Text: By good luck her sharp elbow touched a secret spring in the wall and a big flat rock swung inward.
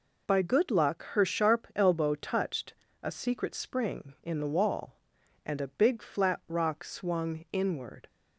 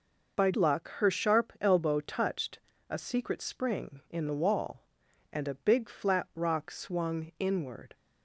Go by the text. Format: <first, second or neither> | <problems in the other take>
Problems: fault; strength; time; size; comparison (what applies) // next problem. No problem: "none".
first | skips "good"; at 0.5 s // pauses between "touched" and "a"; slight; at 2.5 s; 0.30 s long; slight in the first